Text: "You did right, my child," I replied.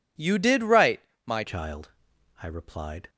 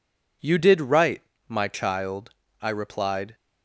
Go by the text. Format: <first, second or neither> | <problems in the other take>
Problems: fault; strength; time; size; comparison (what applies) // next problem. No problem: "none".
second | changes voice at "child"; from 1.4 s on; 1.6 s long